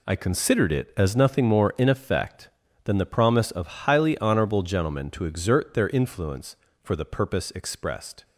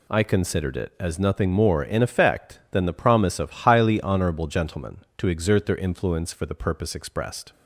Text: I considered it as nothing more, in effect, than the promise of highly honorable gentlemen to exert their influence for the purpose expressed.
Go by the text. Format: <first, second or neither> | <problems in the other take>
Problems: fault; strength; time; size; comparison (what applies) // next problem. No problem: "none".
neither | none